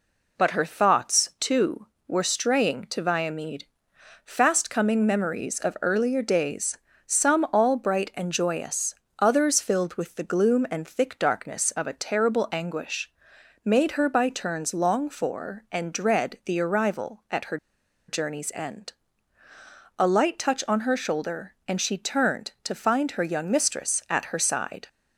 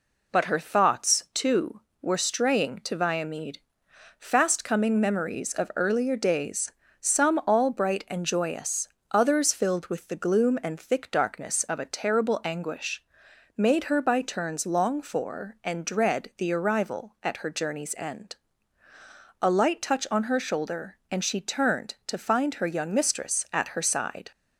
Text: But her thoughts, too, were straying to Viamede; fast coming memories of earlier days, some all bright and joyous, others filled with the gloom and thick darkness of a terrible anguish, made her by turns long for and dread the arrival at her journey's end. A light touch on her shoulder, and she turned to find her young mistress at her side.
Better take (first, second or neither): second